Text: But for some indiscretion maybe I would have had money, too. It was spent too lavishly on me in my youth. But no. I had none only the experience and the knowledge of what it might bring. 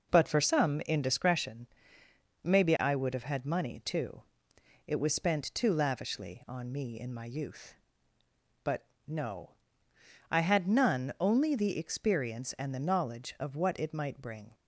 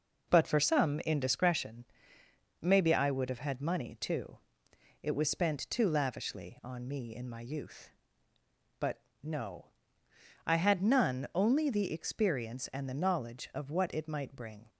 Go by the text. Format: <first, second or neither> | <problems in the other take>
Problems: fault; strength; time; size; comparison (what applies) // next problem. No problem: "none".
neither | pauses between "indiscretion" and "maybe"; noticeable; the same in both // pauses between "But" and "no"; slight; the same in both